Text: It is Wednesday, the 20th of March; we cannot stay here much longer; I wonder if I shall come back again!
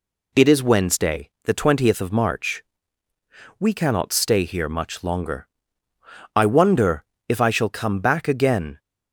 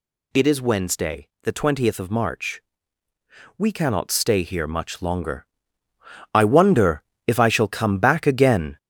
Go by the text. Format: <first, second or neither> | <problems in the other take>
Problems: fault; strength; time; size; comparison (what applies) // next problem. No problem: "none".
first | gets louder; noticeable; throughout; 5 dB // pauses between "wonder" and "if"; slight; at 7.0 s; 0.26 s long; slight in the first